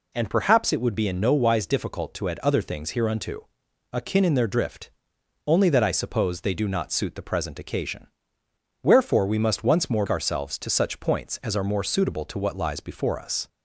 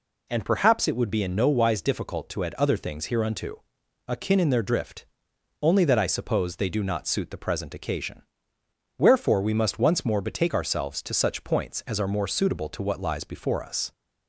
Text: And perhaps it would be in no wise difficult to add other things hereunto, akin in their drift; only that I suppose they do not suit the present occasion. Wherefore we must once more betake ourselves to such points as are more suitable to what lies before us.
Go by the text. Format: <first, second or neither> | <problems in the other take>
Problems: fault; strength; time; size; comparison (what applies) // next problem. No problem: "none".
second | skips "betake"; at 10.0 s